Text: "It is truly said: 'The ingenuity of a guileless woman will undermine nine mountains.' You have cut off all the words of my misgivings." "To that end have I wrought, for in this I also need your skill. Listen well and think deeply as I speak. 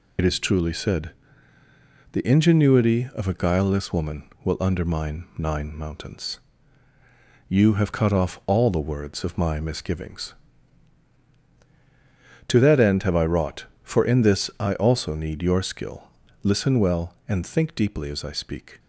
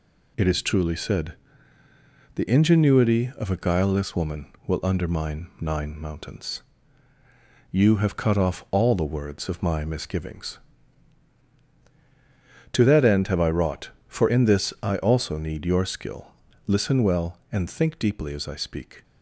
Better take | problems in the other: second | loses the start of "It"; at 0.1 s; 55 ms

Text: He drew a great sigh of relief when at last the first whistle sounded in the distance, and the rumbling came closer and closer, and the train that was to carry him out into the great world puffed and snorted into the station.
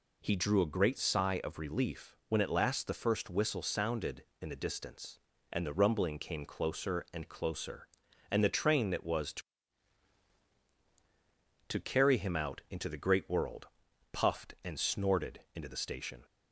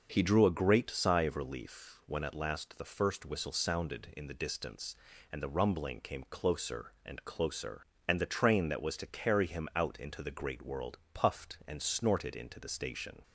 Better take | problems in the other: second | says "to" twice; at 11.6 s // pauses between "world" and "puffed"; at 13.6 s; 0.44 s long

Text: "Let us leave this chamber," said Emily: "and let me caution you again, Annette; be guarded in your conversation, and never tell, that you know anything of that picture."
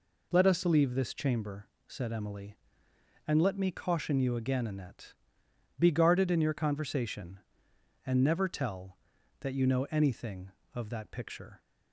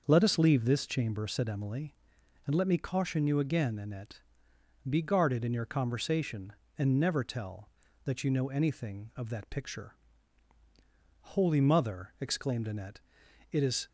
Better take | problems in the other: first | starts louder than the rest; until 1.0 s; 6 dB // goes on to say "Holy Mother exclaimed Annette it is"; strong; from 11.2 s on; 2.6 s long

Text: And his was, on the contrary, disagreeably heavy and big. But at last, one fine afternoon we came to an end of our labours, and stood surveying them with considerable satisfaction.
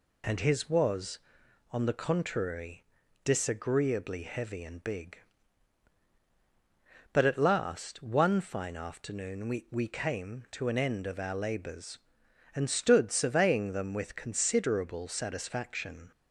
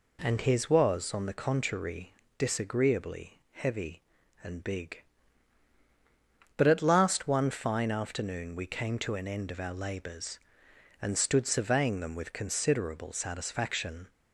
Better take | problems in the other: second | says "we" twice; at 9.7 s

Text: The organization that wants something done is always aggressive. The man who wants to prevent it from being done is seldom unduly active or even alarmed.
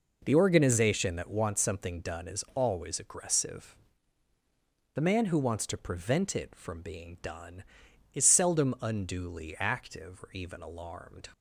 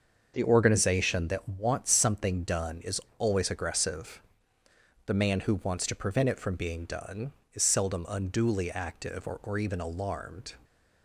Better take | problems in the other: first | starts louder than the rest; until 1.3 s; 6.5 dB // pauses between "is" and "always"; slight; at 2.9 s; 0.20 s long // says "or" twice; at 9.4 s

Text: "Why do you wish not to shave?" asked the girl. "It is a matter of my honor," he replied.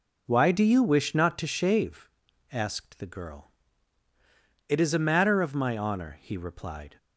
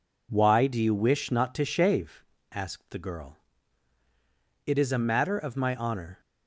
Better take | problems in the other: first | stops before "he replied"; at 6.1 s

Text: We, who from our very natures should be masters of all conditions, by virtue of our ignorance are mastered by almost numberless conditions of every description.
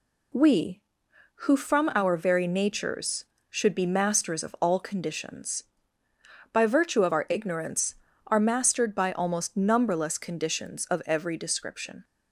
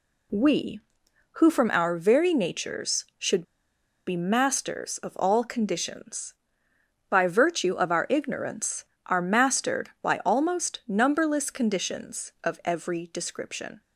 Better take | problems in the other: first | pauses between "should" and "be"; noticeable; at 3.4 s; 0.64 s long

